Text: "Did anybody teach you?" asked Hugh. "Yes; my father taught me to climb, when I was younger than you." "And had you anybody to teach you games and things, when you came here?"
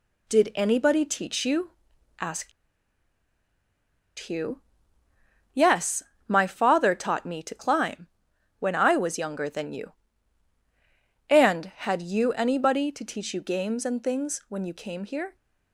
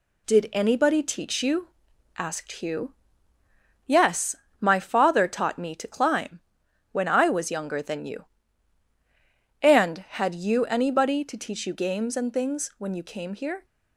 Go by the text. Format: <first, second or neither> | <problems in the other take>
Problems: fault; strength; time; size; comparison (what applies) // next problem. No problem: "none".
second | pauses between "asked" and "Hugh"; strong; at 2.5 s; 1.6 s long